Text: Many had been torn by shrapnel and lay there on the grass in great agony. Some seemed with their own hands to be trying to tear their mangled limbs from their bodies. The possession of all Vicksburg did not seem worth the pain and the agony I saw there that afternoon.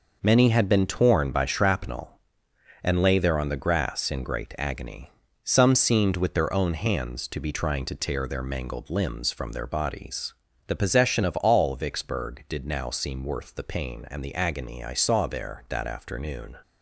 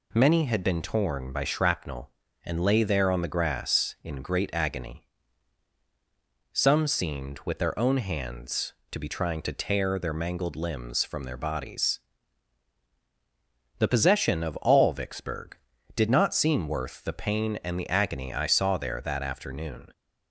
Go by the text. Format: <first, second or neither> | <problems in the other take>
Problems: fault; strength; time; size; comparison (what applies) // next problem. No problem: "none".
second | says "now" for "not"; at 12.6 s